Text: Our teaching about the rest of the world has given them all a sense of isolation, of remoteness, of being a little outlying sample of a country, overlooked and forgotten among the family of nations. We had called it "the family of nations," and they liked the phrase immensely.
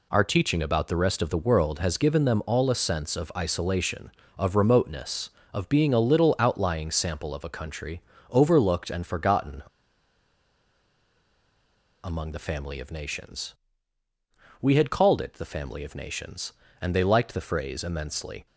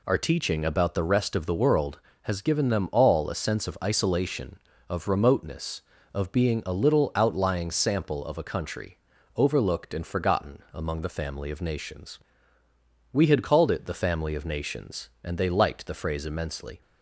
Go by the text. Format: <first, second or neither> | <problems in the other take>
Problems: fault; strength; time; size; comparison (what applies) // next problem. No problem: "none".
second | pauses between "forgotten" and "among"; strong; at 9.6 s; 2.4 s long